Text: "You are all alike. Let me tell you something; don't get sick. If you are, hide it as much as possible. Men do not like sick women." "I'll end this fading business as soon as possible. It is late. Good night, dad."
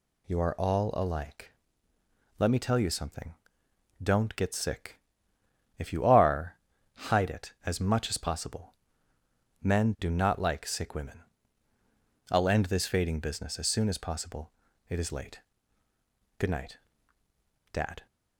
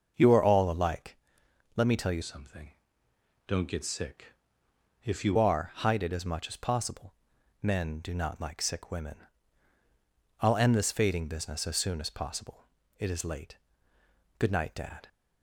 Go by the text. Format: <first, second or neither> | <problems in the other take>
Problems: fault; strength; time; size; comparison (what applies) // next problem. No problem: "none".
first | starts louder than the rest; noticeable; until 1.1 s; 6 dB // changes voice from "something" to "you"; from 2.2 to 5.3 s; 3.1 s long